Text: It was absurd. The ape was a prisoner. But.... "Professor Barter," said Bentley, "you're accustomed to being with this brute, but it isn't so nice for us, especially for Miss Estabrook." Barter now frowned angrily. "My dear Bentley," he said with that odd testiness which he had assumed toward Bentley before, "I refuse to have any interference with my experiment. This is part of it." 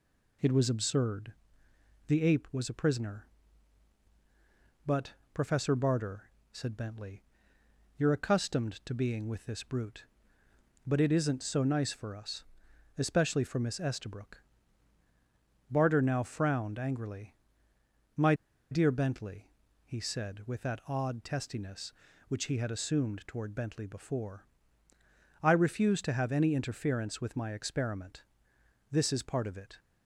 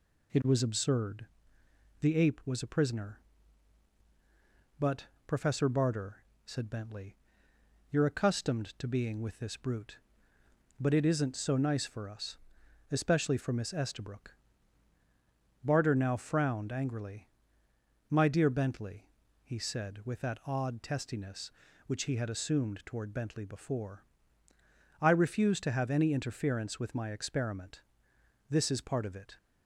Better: second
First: pauses between "My" and "dear"; at 18.3 s; 0.37 s long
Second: none

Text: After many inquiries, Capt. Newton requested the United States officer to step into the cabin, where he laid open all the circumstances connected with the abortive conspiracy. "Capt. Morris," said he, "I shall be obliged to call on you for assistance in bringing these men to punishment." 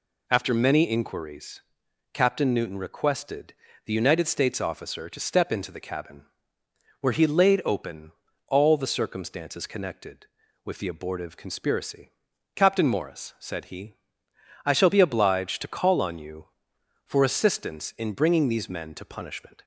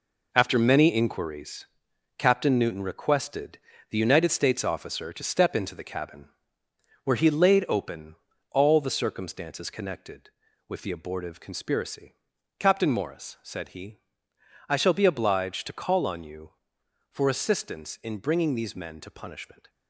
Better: first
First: pauses between "requested" and "the"; slight; at 3.5 s; 0.32 s long // pauses between "open" and "all"; at 8.1 s; 0.38 s long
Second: gets quieter; strong; throughout; 8.5 dB // pauses between "requested" and "the"; slight; at 3.5 s; 0.32 s long // pauses between "open" and "all"; at 8.1 s; 0.38 s long

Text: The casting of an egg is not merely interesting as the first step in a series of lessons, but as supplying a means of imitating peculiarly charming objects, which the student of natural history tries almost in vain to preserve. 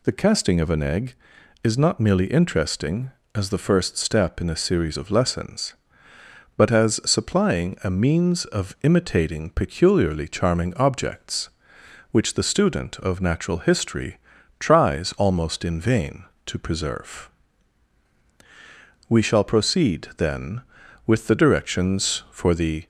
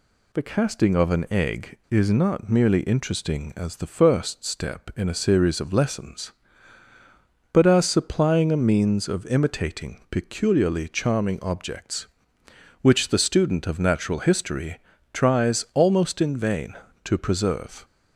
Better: second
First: pauses between "history" and "tries"; at 14.1 s; 0.40 s long // goes on to say "We shall proceed then with the directions for the"; strong; from 19.0 s on; 3.7 s long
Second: pauses between "history" and "tries"; slight; at 14.7 s; 0.34 s long

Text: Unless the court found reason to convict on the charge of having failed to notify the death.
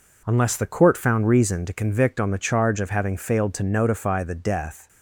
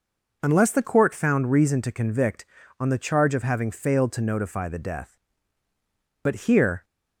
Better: first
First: none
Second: goes on to say "But here"; noticeable; from 6.2 s on; 0.62 s long

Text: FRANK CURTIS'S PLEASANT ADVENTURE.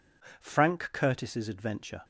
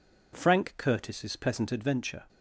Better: second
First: skips "PLEASANT"; at 1.4 s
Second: none

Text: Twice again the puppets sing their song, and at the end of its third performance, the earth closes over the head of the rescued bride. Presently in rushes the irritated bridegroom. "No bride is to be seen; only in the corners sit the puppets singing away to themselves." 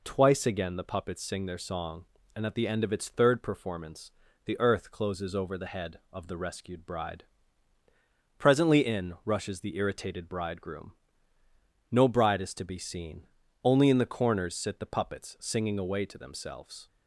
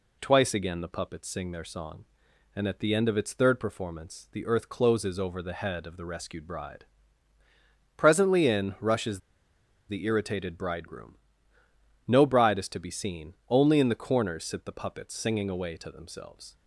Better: first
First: none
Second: pauses between "rushes" and "the"; noticeable; at 9.2 s; 0.68 s long

